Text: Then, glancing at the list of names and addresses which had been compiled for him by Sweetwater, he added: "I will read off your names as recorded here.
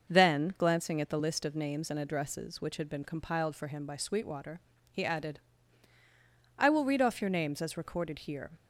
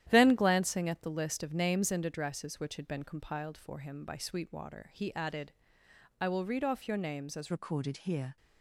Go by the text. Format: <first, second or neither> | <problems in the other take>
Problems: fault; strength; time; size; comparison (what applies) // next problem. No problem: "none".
first | starts louder than the rest; strong; until 1.1 s; 11.5 dB; noticeable in the first // changes voice at "recorded"; from 7.5 s on; 0.8 s long